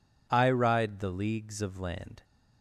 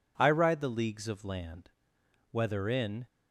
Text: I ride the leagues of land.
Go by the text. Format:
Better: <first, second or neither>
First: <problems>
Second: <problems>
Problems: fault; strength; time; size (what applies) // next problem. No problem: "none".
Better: first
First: none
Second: goes on to say "Whether in"; noticeable; from 2.3 s on; 0.74 s long